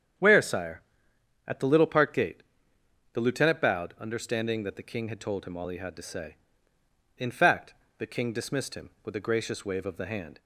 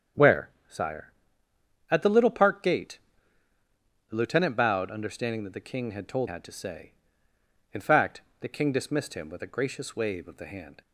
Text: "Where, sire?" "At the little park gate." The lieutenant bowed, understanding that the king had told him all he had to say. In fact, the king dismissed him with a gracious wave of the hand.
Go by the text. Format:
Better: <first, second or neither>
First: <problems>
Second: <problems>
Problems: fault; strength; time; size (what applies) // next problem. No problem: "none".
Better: first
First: starts louder than the rest; strong; until 1.8 s; 8.5 dB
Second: starts louder than the rest; strong; until 2.1 s; 7.5 dB // skips "him all he"; at 6.2 s